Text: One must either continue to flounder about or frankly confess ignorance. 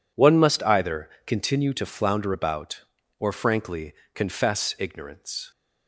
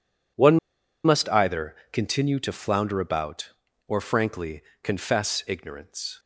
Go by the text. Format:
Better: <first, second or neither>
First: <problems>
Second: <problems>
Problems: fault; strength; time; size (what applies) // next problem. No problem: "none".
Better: first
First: pauses between "either" and "continue"; slight; at 1.0 s; 0.16 s long // pauses between "frankly" and "confess"; slight; at 3.9 s; 0.22 s long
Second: pauses between "One" and "must"; noticeable; at 0.5 s; 0.46 s long // pauses between "either" and "continue"; slight; at 1.7 s; 0.16 s long // pauses between "frankly" and "confess"; slight; at 4.6 s; 0.22 s long